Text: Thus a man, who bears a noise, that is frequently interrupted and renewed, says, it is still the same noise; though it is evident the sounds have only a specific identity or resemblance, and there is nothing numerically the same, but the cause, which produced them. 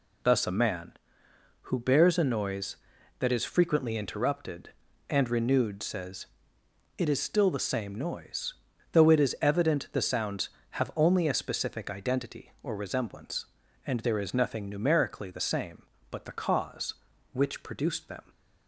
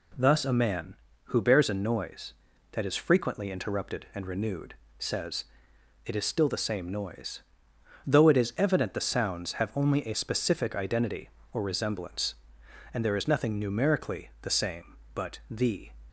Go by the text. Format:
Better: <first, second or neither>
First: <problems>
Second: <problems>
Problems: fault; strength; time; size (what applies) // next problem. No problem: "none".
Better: first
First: none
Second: stops before "cause which produced them"; at 16.0 s